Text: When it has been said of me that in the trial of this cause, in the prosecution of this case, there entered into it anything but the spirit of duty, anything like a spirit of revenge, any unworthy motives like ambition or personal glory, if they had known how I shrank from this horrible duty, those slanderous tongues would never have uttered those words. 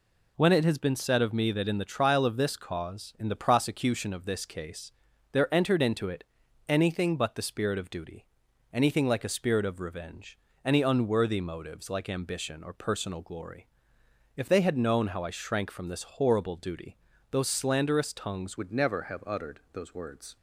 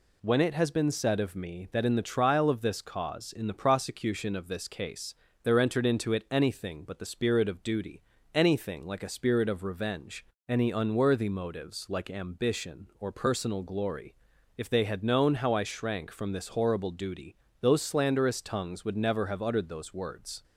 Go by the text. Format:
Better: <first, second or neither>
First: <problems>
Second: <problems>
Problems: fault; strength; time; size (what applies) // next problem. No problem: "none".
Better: second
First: pauses between "it" and "anything"; at 6.2 s; 0.42 s long // changes voice at "would"; from 18.5 s on; 1.8 s long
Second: none